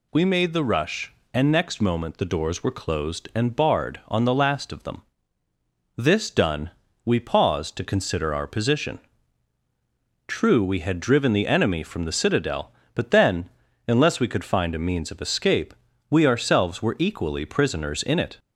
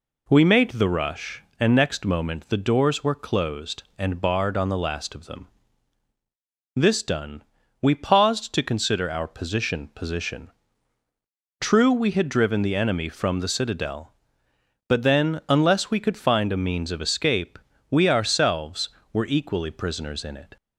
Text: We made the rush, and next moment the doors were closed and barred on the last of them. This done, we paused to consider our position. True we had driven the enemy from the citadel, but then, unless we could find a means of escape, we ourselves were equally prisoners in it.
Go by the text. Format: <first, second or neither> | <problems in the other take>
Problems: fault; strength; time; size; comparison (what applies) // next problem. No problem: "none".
first | says "position" twice; at 9.9 s